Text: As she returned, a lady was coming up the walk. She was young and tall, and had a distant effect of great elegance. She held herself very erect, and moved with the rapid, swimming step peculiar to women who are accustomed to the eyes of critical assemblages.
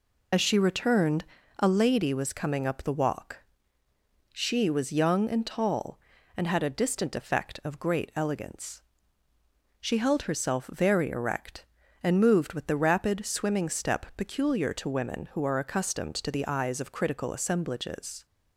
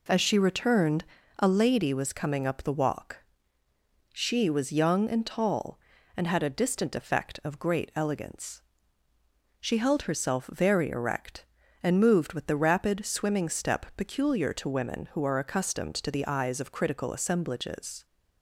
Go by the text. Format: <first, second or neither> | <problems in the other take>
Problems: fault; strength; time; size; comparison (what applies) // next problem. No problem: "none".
second | loses the start of "As"; at 0.3 s; 65 ms